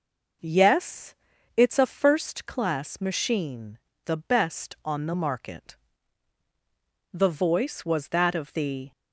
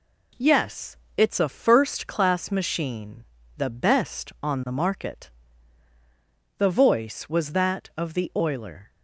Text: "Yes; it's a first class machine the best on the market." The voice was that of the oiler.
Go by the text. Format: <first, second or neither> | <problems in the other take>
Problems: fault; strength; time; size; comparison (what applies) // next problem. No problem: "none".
second | pauses between "machine" and "the"; slight; at 3.7 s; 0.28 s long; slight in the second // stops before "oiler"; at 8.9 s